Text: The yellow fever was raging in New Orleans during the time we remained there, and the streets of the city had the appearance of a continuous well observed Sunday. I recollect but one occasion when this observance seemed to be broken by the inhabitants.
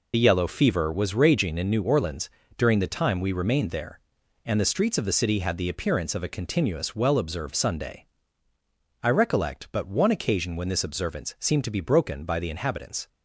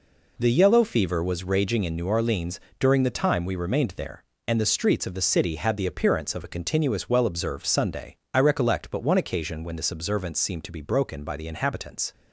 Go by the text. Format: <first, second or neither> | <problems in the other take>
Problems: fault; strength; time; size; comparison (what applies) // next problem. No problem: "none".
second | loses the start of "The"; at 0.1 s; 40 ms // pauses between "Orleans" and "during"; slight; at 2.2 s; 0.26 s long; slight in the second